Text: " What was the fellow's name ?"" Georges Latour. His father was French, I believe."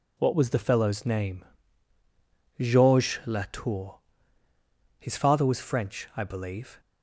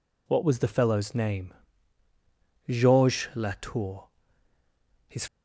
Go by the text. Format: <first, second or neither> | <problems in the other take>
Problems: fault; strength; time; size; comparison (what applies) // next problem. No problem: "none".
first | stops before "father was French I believe"; at 5.2 s